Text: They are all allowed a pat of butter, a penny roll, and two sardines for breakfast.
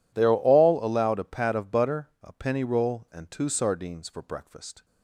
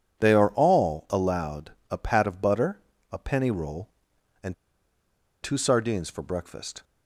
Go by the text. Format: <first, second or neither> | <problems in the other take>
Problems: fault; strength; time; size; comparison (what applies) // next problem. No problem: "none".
first | pauses between "allowed" and "a"; slight; at 1.7 s; 0.18 s long // pauses between "and" and "two"; noticeable; at 4.5 s; 0.88 s long